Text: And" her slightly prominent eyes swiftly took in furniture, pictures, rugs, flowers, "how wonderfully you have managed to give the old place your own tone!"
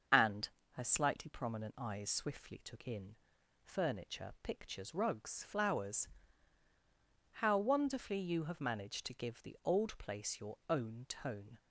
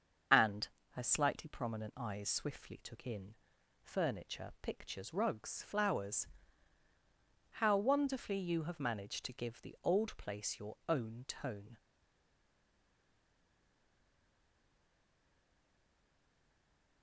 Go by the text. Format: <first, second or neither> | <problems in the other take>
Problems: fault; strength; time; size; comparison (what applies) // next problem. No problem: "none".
first | starts louder than the rest; until 1.5 s; 7 dB; also in the first // pauses between "And" and "her"; slight; at 0.6 s; 0.24 s long; slight in the first // pauses between "in" and "furniture"; noticeable; at 3.3 s; 0.48 s long; noticeable in the first // stays silent after the last word; strong; from 11.7 s on; 5.3 s long